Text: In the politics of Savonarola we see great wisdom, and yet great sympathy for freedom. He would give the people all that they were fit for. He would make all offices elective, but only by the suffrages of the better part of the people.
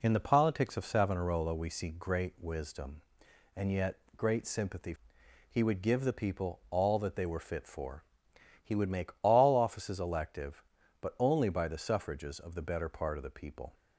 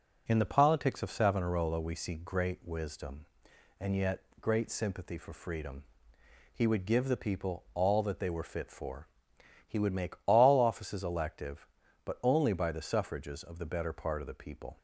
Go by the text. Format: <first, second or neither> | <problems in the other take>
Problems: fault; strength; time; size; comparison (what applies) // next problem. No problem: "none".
second | pauses between "yet" and "great"; slight; at 3.9 s; 0.20 s long; slight in the second // skips "for freedom"; at 5.2 s